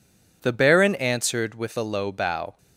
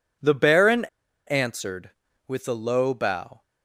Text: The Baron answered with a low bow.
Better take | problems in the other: first | pauses between "Baron" and "answered"; at 0.8 s; 0.42 s long

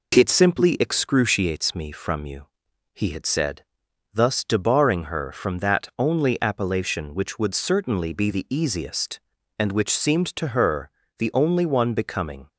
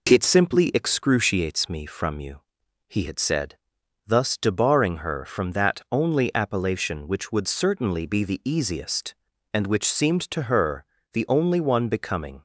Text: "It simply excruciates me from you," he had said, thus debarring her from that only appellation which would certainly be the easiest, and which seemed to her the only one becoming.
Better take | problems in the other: neither | pauses between "her" and "the"; slight; the same in both

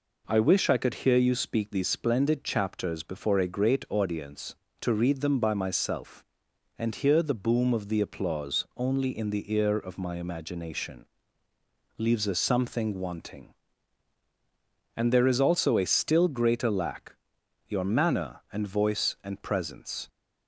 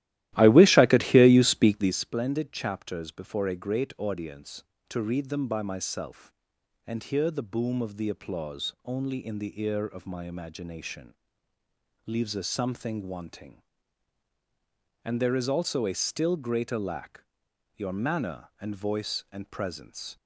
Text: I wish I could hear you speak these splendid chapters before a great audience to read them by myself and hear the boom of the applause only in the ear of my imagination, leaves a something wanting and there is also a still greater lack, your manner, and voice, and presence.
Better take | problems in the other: first | starts louder than the rest; strong; until 2.0 s; 14.5 dB

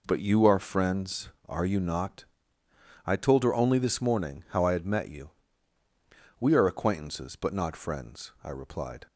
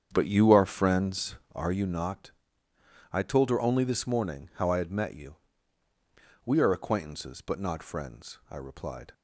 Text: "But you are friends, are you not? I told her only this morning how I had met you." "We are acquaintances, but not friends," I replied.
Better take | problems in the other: first | starts louder than the rest; strong; until 1.7 s; 8 dB

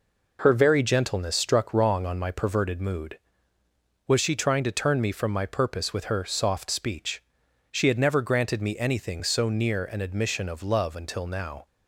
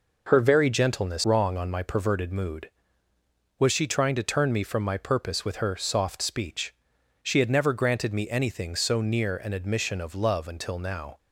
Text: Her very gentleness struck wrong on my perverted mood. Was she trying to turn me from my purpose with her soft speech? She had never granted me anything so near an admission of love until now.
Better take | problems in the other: first | skips "struck"; at 1.2 s

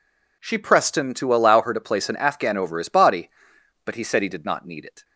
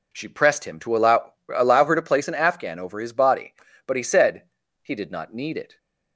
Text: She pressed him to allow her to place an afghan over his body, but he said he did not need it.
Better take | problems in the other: first | says "allow" twice; at 1.5 s // pauses between "said" and "he"; at 4.4 s; 0.40 s long

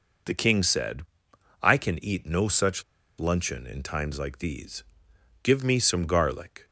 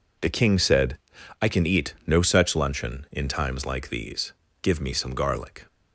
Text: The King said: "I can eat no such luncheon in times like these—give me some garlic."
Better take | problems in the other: second | pauses between "such" and "luncheon"; at 2.8 s; 0.37 s long

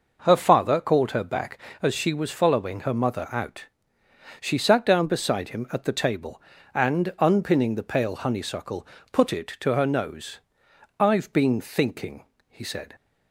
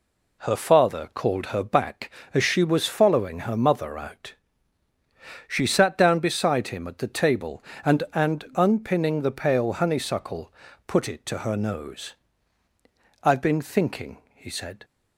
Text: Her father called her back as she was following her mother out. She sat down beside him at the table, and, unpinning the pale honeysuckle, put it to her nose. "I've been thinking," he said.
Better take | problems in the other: first | says "and" twice; at 8.1 s

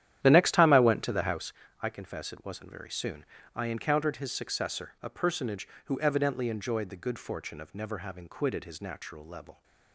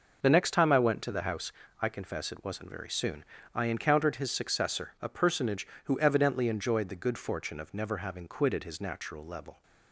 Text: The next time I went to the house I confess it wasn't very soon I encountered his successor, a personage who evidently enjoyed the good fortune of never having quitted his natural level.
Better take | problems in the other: second | starts louder than the rest; strong; until 1.5 s; 11 dB // pauses between "house" and "I"; slight; at 1.5 s; 0.30 s long; slight in the second // pauses between "soon" and "I"; slight; at 3.2 s; 0.30 s long; slight in the second

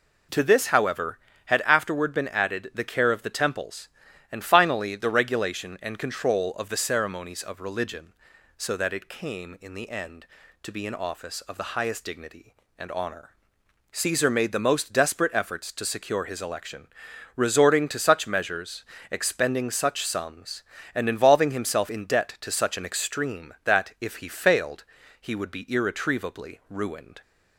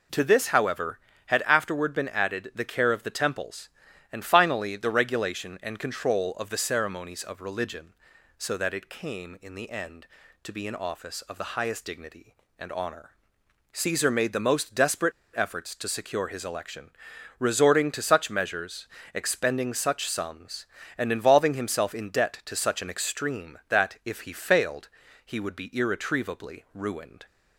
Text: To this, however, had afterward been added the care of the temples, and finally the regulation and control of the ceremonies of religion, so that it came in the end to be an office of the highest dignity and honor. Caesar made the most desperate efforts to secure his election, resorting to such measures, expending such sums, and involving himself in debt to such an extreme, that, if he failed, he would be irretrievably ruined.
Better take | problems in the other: first | pauses between "desperate" and "efforts"; slight; at 15.1 s; 0.23 s long

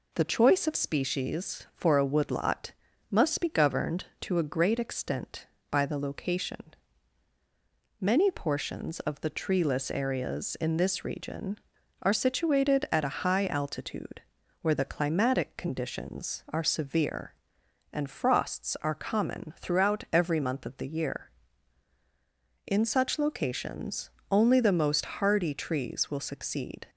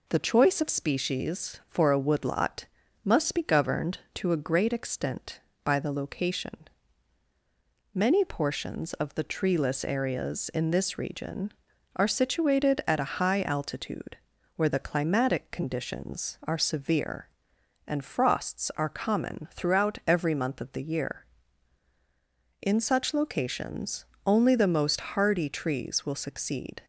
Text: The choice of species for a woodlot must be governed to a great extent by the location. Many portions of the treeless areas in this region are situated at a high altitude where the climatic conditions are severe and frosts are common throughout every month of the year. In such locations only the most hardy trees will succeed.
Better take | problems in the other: neither | pauses between "woodlot" and "must"; the same in both // pauses between "altitude" and "where"; the same in both // pauses between "locations" and "only"; slight; the same in both

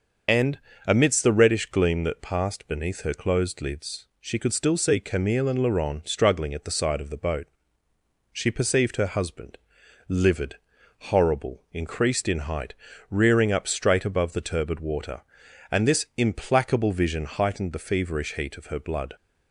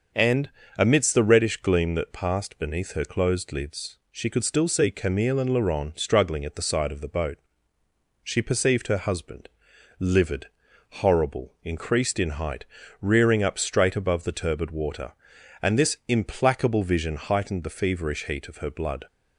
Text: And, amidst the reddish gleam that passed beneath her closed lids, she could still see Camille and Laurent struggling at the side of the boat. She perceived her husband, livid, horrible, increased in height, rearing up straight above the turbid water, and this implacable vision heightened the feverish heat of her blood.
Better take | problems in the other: second | loses the start of "And"; at 0.2 s; 50 ms // starts louder than the rest; until 1.5 s; 6 dB; also in the second

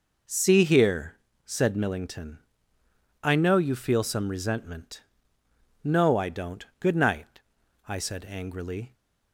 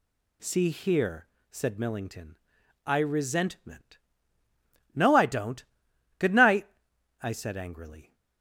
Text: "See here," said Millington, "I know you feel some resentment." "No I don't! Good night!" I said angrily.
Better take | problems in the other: first | skips "know you feel some"; at 2.9 s

